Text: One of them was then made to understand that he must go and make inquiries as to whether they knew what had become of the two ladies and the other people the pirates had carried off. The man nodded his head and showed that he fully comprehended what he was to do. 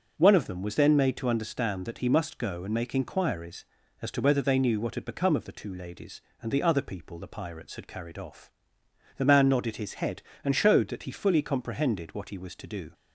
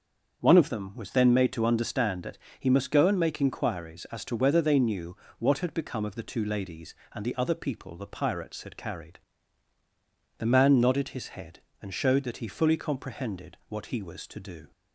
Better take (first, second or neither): first